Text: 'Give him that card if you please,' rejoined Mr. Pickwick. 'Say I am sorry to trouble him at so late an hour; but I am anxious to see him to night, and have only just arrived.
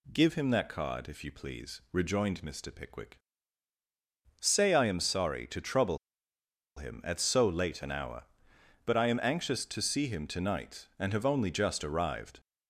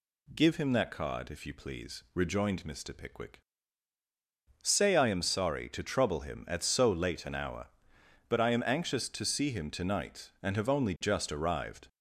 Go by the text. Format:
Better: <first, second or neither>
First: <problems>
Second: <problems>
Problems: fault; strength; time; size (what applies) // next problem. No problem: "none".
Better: second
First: pauses between "trouble" and "him"; noticeable; at 5.9 s; 0.79 s long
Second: none